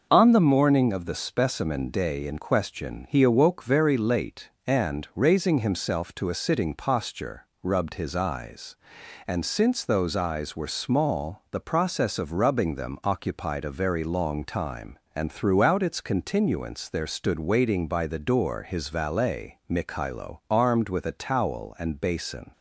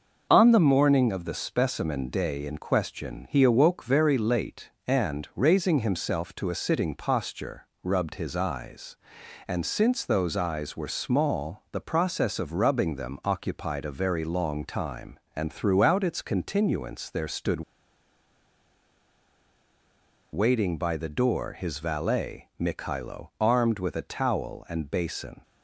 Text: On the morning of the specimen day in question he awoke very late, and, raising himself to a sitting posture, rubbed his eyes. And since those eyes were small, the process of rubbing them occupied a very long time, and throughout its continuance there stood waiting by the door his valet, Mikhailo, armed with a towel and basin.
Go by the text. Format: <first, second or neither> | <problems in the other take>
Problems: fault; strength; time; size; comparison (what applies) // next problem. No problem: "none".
first | pauses between "stood" and "waiting"; strong; at 17.6 s; 2.7 s long